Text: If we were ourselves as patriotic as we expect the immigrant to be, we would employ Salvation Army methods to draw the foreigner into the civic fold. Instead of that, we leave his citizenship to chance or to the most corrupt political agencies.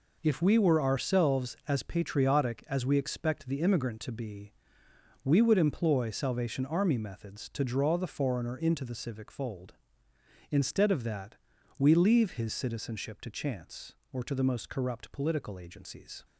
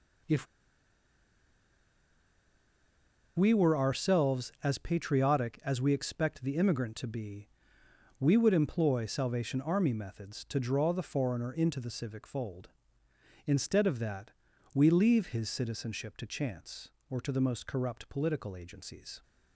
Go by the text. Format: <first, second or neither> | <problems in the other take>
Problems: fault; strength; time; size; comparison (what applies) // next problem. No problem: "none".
first | pauses between "If" and "we"; strong; at 0.4 s; 2.9 s long